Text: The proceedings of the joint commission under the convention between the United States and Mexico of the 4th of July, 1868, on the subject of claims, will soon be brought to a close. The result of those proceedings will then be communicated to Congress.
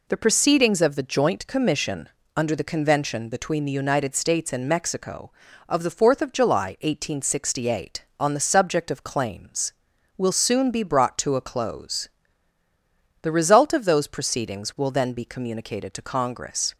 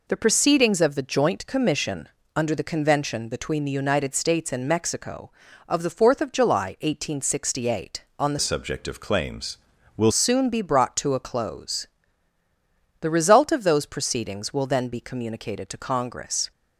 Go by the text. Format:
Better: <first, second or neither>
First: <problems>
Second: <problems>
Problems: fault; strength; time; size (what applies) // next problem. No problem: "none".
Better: first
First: pauses between "commission" and "under"; slight; at 2.0 s; 0.26 s long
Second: pauses between "commission" and "under"; slight; at 2.0 s; 0.26 s long // changes voice from "subject" to "will"; from 8.4 to 10.1 s; 1.7 s long